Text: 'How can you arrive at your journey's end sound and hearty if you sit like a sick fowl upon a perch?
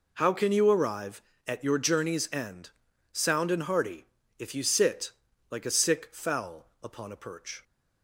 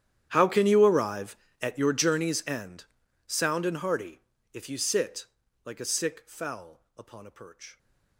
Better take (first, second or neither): first